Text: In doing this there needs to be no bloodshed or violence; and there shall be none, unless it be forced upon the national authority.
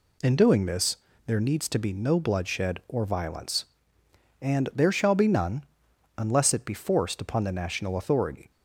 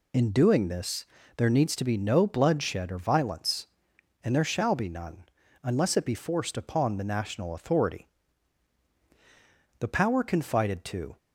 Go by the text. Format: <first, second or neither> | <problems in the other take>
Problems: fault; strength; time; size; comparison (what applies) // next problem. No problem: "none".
first | pauses between "this" and "there"; slight; at 1.0 s; 0.32 s long; slight in the first // goes on to say "The power confided to"; from 9.8 s on; 1.3 s long